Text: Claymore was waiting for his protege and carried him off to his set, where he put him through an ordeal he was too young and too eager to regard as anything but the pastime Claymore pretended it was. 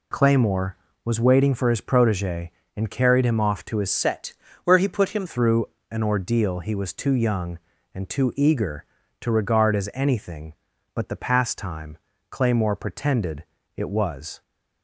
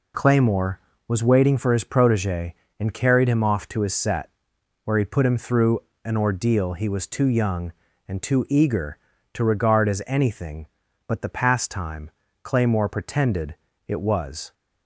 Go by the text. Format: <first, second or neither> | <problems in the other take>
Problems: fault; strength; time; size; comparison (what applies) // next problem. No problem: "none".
second | changes voice from "set" to "him"; from 3.8 to 5.2 s; 1.4 s long // pauses between "through" and "an"; slight; at 5.6 s; 0.26 s long; slight in the second // pauses between "pastime" and "Claymore"; slight; at 11.9 s; 0.34 s long; slight in the second // pauses between "pretended" and "it"; slight; at 13.4 s; 0.32 s long; slight in the second